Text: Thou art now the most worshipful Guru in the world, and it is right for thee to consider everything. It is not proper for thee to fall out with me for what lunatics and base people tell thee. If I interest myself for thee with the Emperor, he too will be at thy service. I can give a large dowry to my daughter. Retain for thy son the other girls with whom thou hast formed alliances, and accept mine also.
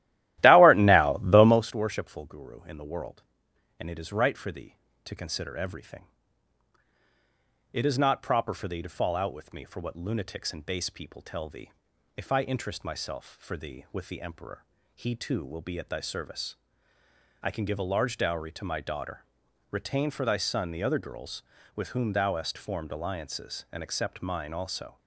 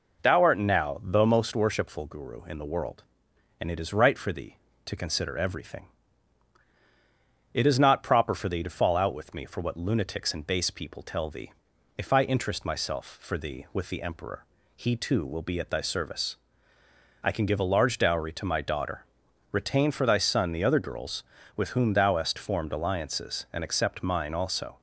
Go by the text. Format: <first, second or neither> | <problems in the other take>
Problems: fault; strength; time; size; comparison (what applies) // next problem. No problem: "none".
second | starts louder than the rest; strong; until 1.7 s; 15 dB